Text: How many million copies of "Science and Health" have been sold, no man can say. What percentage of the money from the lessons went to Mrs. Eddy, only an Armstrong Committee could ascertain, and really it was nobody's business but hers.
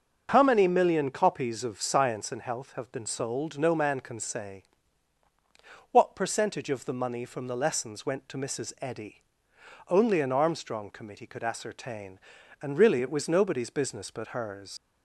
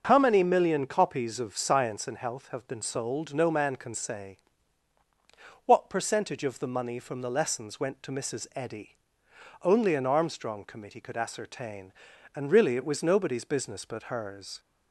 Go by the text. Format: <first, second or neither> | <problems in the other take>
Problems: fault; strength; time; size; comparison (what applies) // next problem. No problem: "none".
second | starts louder than the rest; until 1.3 s; 6.5 dB; also in the second // leaves "hers" unfinished; at 14.7 s; 60 ms